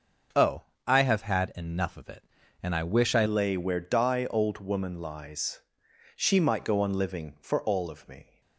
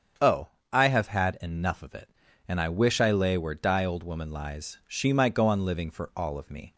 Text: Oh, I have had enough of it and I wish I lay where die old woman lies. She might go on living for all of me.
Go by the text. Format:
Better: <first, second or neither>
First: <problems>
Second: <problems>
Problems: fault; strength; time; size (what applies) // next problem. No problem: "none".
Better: second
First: starts louder than the rest; until 1.6 s; 6.5 dB // changes voice at "lay"; from 3.2 s on; 5.2 s long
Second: starts louder than the rest; strong; until 1.5 s; 7.5 dB